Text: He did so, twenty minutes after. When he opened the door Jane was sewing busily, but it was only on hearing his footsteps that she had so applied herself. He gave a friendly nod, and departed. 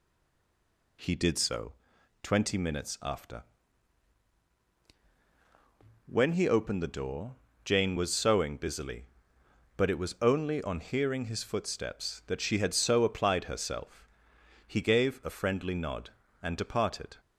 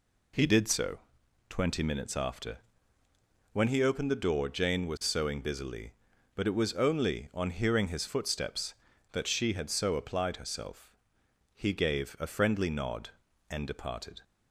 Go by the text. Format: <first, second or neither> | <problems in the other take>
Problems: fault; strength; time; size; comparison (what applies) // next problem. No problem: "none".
second | stays silent before the first word; until 0.9 s; 0.9 s long // pauses between "door" and "Jane"; slight; at 7.3 s; 0.28 s long